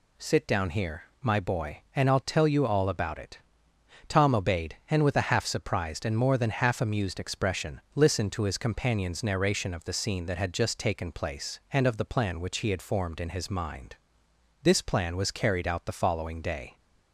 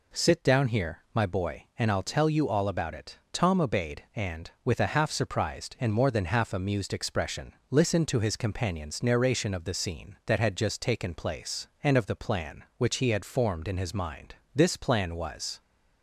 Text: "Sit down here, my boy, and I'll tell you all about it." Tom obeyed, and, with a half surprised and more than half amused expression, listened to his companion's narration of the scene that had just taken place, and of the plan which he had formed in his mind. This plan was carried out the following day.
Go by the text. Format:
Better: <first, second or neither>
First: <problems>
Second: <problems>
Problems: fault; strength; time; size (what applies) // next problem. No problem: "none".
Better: first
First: none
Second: stops before "carried out the following day"; at 15.6 s